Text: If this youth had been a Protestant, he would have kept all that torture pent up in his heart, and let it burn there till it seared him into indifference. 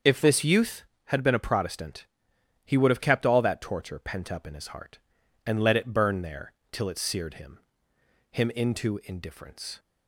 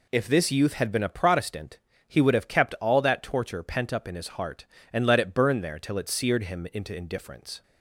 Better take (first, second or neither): second